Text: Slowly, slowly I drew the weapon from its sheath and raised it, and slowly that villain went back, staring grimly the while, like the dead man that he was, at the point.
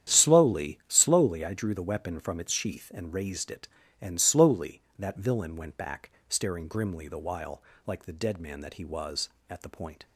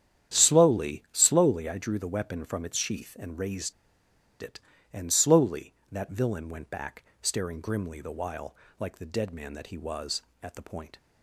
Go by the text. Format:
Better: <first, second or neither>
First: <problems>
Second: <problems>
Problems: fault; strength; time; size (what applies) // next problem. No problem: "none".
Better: first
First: starts louder than the rest; strong; until 1.2 s; 9.5 dB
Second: starts louder than the rest; strong; until 1.4 s; 9.5 dB // pauses between "raised" and "it"; noticeable; at 3.7 s; 0.69 s long